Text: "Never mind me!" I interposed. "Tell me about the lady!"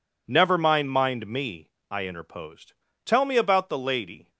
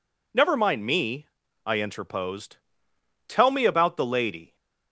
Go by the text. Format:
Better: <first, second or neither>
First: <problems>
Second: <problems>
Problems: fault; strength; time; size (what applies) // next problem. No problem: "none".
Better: second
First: says "mind" twice; at 0.8 s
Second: none